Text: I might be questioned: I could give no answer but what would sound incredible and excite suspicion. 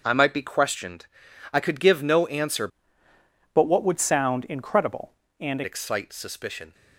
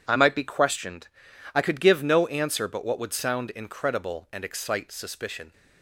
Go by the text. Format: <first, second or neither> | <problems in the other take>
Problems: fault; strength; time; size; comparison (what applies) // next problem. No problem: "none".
second | starts louder than the rest; until 1.0 s; 6.5 dB // changes voice from "but" to "and"; from 3.5 to 5.6 s; 2.1 s long